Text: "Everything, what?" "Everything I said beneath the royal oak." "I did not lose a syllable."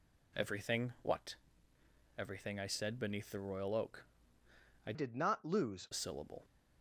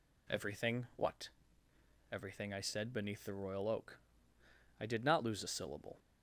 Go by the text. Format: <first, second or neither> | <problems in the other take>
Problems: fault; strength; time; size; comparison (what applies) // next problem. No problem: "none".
second | changes voice from "did" to "lose"; from 4.9 to 5.8 s; 0.9 s long